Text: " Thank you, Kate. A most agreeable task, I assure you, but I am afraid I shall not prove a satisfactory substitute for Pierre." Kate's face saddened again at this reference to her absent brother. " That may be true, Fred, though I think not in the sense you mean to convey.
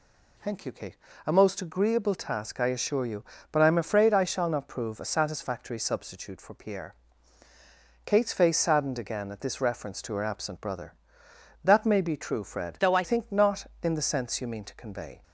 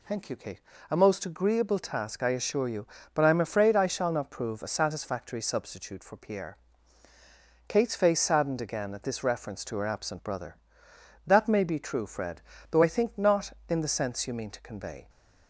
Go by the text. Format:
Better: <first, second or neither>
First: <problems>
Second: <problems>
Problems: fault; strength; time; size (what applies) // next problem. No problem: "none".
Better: second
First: changes voice from "though" to "I"; from 12.7 to 13.0 s; 0.3 s long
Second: none